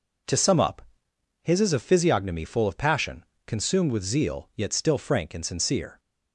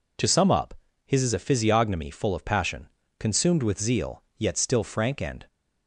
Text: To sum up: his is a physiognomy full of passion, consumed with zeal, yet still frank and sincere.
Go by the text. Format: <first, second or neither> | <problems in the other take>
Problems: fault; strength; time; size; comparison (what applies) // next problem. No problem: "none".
first | stops before "sincere"; at 5.4 s